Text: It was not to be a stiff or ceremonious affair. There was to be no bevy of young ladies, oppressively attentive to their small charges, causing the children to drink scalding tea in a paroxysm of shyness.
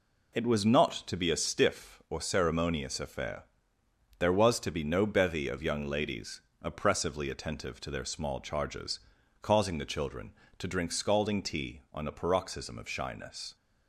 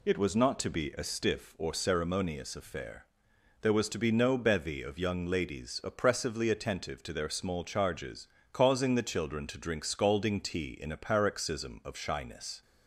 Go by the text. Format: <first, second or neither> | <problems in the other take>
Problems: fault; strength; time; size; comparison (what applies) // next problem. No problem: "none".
second | says "on" for "in"; at 11.9 s